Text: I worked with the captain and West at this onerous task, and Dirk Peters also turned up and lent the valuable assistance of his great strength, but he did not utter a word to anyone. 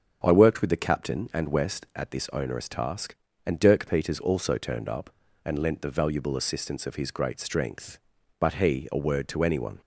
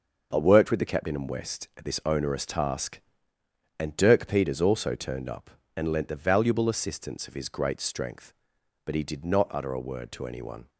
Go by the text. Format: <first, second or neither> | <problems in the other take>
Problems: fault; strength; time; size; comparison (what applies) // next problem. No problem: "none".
second | starts louder than the rest; until 1.2 s; 6.5 dB; noticeable in the second // skips "did not utter"; at 8.8 s